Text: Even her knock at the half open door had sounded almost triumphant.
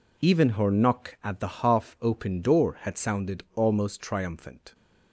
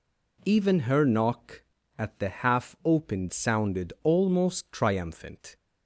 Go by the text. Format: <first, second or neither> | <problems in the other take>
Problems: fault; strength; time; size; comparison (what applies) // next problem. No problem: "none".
first | skips "door had"; at 3.2 s